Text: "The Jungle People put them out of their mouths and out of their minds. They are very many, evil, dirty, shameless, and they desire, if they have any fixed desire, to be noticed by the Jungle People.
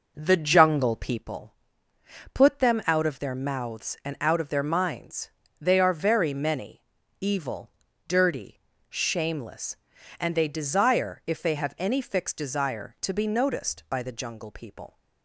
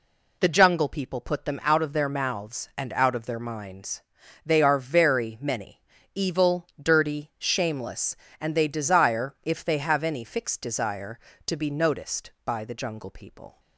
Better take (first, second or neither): second